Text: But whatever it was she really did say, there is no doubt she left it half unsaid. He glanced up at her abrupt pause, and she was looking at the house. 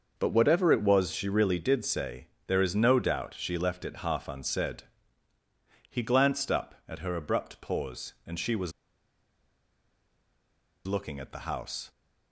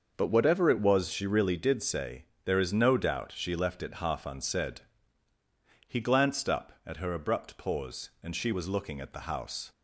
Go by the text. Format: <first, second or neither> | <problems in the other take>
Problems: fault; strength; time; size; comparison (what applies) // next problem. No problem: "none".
second | starts louder than the rest; noticeable; until 1.1 s; 6 dB; noticeable in the second // pauses between "was" and "looking"; strong; at 8.7 s; 2.1 s long